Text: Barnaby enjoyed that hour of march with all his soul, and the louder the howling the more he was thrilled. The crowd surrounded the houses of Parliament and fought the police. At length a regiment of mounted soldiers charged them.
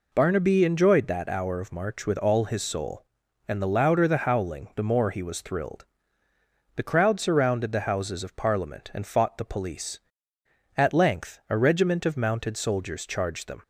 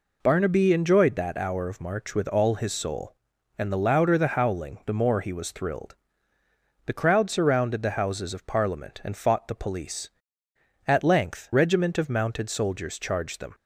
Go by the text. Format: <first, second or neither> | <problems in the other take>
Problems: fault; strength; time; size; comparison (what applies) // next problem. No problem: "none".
first | skips "a"; at 11.5 s